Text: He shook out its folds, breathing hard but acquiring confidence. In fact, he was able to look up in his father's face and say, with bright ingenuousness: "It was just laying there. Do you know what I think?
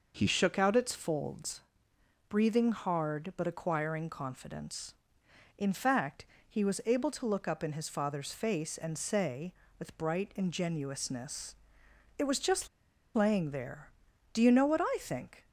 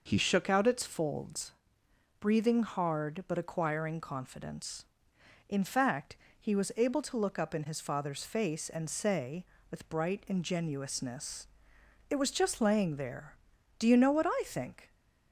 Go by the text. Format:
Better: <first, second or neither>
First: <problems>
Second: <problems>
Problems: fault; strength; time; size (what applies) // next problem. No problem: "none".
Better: second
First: pauses between "just" and "laying"; noticeable; at 12.6 s; 0.47 s long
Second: none